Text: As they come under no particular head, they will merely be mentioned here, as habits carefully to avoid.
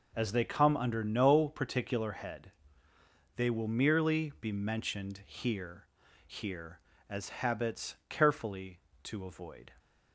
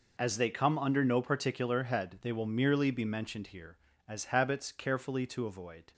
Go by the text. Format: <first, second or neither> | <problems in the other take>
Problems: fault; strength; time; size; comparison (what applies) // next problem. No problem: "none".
second | says "here" twice; at 6.2 s